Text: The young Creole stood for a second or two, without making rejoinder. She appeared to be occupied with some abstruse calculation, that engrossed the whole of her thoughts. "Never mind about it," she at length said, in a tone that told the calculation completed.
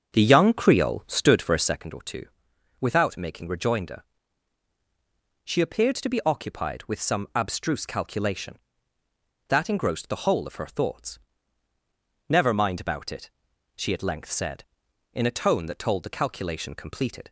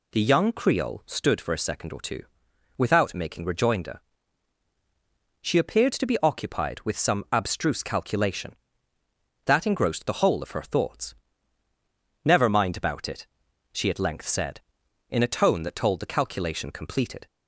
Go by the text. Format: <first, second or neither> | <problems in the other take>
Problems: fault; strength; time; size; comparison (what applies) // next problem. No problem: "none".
second | starts louder than the rest; strong; until 1.8 s; 7 dB